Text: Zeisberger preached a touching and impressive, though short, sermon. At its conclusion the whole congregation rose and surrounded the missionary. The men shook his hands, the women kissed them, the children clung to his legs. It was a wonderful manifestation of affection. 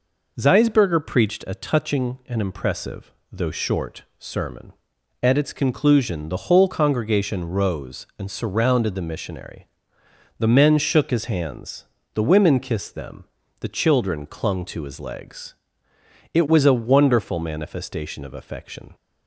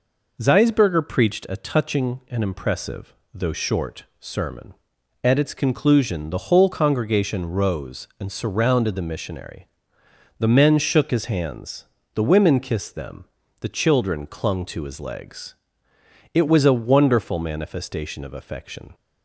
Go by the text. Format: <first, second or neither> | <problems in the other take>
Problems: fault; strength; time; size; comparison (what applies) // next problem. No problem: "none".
neither | none